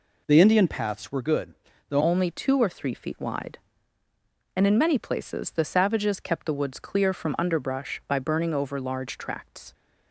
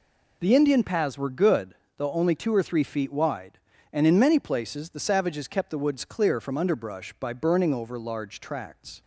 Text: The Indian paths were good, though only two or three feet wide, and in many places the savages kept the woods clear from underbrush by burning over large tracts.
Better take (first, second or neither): second